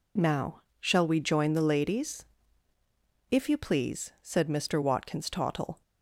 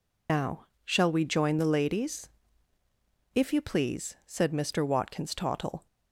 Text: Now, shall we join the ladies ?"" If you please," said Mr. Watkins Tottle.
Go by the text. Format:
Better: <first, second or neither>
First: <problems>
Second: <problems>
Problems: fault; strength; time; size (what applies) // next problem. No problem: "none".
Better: first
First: none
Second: loses the start of "Now"; at 0.2 s; 95 ms